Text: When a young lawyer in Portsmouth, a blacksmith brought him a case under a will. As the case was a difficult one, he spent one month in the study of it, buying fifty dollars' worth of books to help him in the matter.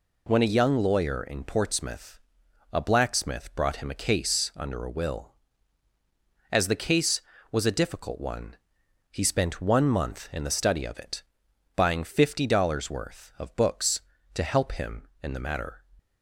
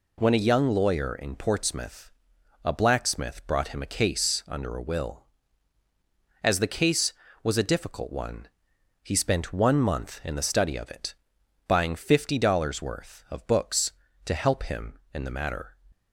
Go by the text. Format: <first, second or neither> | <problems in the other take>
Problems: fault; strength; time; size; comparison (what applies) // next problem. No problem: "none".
neither | none